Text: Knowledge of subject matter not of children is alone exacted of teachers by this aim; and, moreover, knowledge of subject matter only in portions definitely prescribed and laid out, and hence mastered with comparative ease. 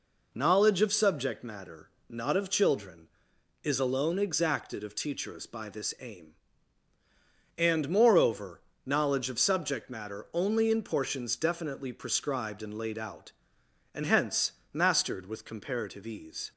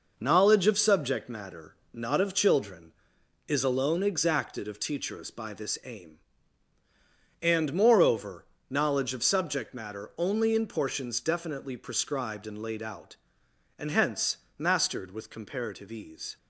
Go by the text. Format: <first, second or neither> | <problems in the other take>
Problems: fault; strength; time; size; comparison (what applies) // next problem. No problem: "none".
first | gets quieter; noticeable; throughout; 6 dB // pauses between "matter" and "not"; slight; at 1.7 s; 0.18 s long; slight in the first // pauses between "hence" and "mastered"; slight; at 14.3 s; 0.20 s long; slight in the first